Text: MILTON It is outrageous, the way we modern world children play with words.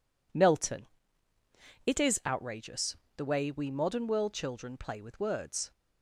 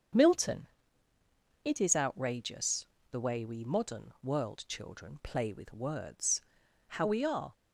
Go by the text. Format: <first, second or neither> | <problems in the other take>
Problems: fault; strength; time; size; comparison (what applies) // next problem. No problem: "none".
first | starts louder than the rest; until 2.1 s; 7 dB // pauses between "MILTON" and "It"; noticeable; at 0.6 s; 0.96 s long; also in the first // goes on to say "How we are"; noticeable; from 6.8 s on; 0.68 s long